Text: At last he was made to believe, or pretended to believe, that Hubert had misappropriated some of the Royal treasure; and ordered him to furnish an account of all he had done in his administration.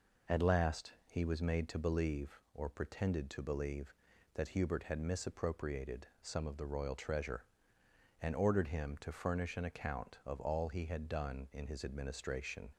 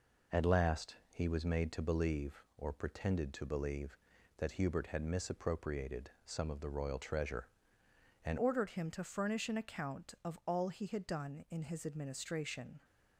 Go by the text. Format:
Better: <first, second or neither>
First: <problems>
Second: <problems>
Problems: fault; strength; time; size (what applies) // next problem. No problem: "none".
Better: first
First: none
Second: changes voice at "ordered"; from 8.3 s on; 4.5 s long